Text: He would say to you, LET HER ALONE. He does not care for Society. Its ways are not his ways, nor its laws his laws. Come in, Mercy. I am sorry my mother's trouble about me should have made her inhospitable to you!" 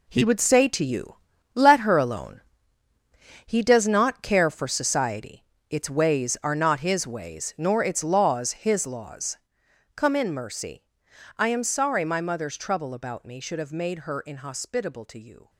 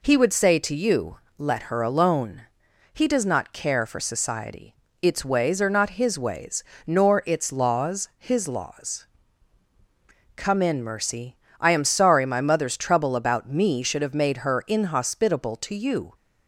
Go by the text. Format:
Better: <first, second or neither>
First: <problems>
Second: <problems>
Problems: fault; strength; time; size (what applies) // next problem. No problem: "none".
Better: second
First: gets quieter; strong; throughout; 10.5 dB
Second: none